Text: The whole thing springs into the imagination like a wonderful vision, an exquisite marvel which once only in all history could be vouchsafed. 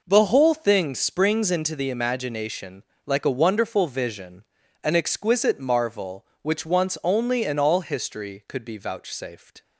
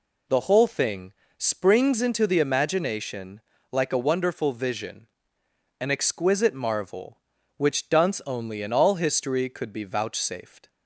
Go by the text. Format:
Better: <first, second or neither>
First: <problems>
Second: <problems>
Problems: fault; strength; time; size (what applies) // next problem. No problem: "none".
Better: first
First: pauses between "imagination" and "like"; slight; at 2.8 s; 0.24 s long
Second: pauses between "thing" and "springs"; slight; at 1.1 s; 0.24 s long // pauses between "imagination" and "like"; slight; at 3.4 s; 0.30 s long // says "dunce" for "once"; at 7.8 s